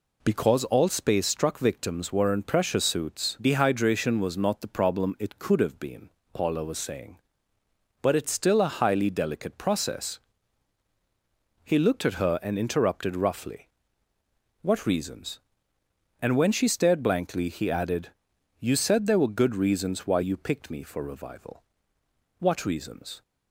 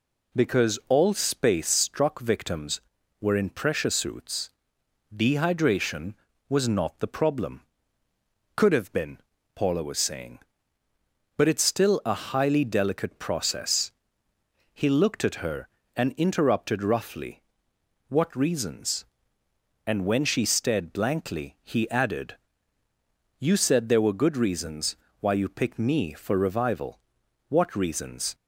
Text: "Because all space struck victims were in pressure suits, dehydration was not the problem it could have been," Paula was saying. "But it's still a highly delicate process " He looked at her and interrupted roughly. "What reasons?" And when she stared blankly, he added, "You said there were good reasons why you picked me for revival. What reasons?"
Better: first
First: none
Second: skips "it"; at 8.0 s // pauses between "reasons" and "why"; slight; at 24.9 s; 0.24 s long

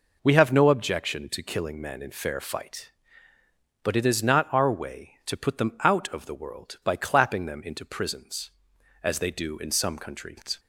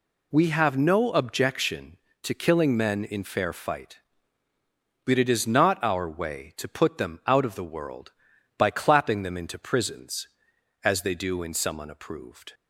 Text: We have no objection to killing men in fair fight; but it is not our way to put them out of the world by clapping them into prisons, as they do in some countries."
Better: first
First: none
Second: says "unapproved" for "countries"; at 11.8 s

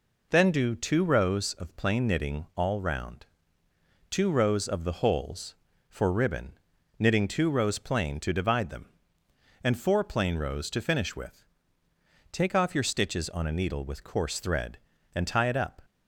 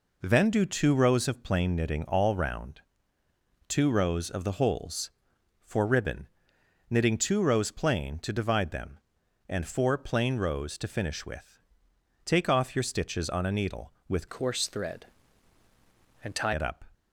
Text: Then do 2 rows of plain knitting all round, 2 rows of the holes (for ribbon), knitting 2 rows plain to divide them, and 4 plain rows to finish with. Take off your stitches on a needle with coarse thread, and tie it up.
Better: first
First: none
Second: changes voice from "coarse" to "tie"; from 14.2 to 16.5 s; 2.3 s long

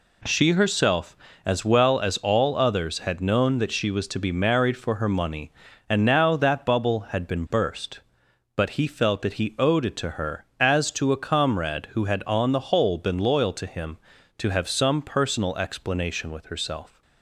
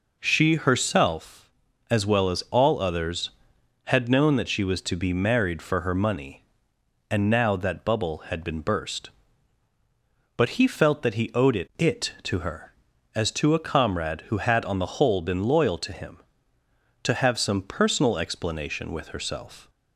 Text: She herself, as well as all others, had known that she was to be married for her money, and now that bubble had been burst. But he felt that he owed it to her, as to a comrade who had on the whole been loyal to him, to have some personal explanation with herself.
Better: first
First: none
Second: says "it" twice; at 11.7 s

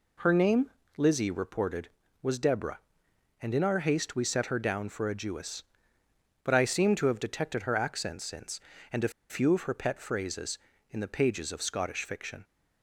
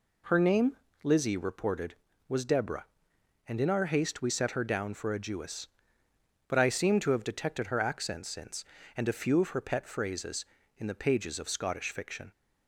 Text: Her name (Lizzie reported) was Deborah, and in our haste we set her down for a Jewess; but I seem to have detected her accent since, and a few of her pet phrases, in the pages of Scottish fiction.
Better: second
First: pauses between "a" and "few"; slight; at 9.1 s; 0.19 s long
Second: none

